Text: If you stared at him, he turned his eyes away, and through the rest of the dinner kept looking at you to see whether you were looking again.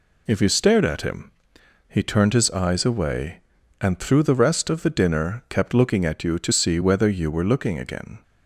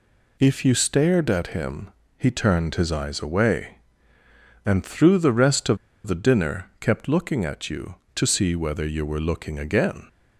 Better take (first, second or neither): first